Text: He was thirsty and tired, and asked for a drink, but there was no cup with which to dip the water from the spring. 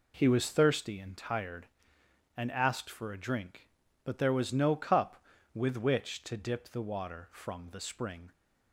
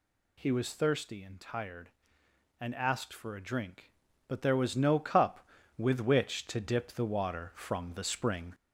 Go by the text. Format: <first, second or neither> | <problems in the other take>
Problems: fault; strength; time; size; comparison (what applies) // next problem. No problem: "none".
first | gets louder; slight; throughout; 3 dB